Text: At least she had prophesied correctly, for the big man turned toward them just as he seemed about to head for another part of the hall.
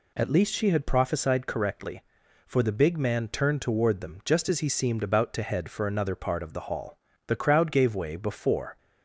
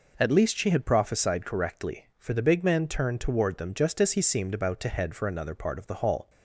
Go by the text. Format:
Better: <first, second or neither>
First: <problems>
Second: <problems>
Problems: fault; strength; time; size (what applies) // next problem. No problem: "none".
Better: second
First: goes on to say "The crowd gave way before"; from 7.2 s on; 1.5 s long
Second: none